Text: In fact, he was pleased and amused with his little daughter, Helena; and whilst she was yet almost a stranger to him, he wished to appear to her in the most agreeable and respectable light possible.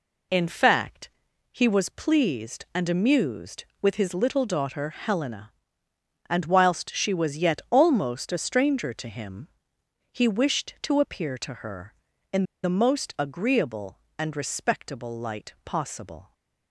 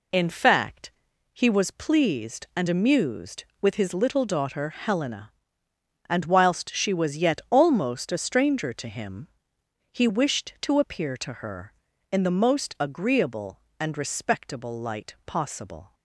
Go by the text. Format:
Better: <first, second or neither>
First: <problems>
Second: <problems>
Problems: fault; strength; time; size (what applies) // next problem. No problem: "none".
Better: second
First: pauses between "in" and "the"; slight; at 12.4 s; 0.20 s long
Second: none